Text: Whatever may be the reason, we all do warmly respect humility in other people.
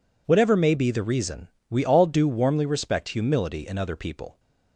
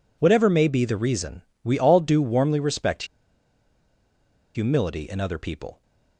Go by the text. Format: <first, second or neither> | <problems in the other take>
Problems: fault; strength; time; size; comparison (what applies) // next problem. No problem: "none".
first | pauses between "respect" and "humility"; strong; at 3.0 s; 1.5 s long